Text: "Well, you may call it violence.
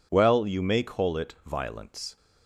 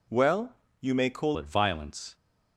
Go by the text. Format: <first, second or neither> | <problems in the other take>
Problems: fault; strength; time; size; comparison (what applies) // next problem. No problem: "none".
first | changes voice at "it"; from 1.3 s on; 0.8 s long